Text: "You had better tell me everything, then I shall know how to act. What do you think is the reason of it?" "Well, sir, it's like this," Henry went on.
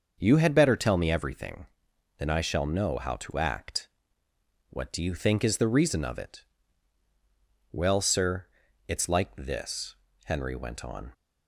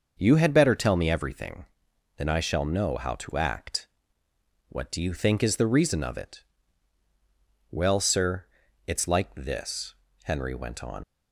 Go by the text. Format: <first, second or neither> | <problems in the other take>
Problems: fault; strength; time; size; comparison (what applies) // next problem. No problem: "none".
first | starts louder than the rest; until 1.1 s; 6 dB; also in the first // leaves "on" unfinished; at 11.0 s; 80 ms